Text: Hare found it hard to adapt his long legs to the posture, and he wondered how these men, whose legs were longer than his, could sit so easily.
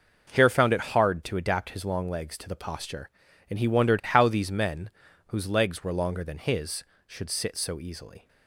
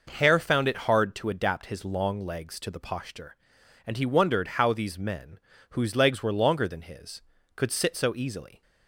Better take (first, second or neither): second